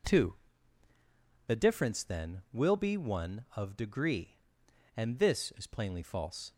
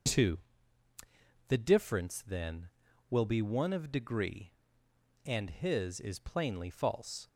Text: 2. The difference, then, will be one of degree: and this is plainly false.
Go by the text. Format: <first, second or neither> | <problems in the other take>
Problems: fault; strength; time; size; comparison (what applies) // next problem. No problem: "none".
first | says "his" for "this"; at 5.4 s